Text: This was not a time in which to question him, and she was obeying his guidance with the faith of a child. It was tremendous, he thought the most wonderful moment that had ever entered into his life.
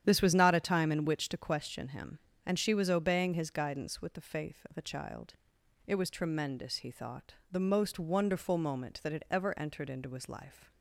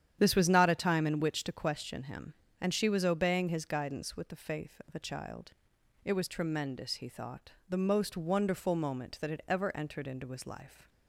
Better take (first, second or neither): neither